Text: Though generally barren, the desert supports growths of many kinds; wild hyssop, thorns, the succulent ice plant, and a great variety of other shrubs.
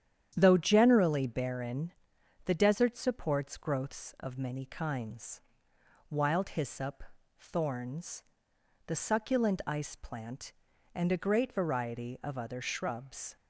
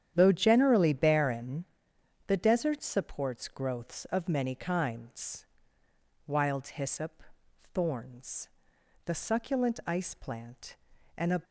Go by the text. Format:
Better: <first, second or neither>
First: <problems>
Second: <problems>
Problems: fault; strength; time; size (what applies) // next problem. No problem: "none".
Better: first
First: starts louder than the rest; strong; until 1.3 s; 9.5 dB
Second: starts louder than the rest; strong; until 1.1 s; 9.5 dB // stops before "great variety of other shrubs"; at 11.4 s